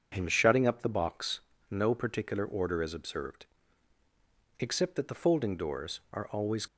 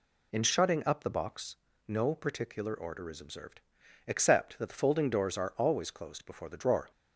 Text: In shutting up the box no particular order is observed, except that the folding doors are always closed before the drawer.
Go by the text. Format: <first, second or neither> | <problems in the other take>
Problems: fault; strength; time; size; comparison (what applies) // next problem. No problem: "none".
second | pauses between "box" and "no"; slight; at 1.3 s; 0.32 s long; slight in the second // stops before "closed before the drawer"; at 6.6 s